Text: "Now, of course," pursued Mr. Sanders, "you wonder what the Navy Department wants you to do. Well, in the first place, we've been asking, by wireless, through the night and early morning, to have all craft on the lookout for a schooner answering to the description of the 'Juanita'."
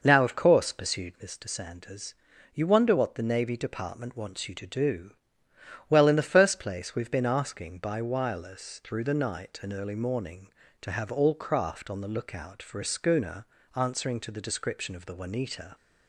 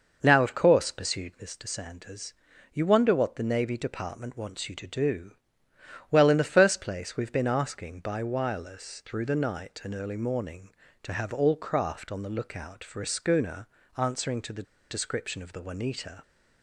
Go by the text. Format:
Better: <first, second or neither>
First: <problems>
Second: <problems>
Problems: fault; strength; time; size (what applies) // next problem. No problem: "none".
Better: first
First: pauses between "schooner" and "answering"; slight; at 13.4 s; 0.30 s long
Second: pauses between "schooner" and "answering"; slight; at 13.6 s; 0.30 s long // pauses between "the" and "description"; slight; at 14.6 s; 0.28 s long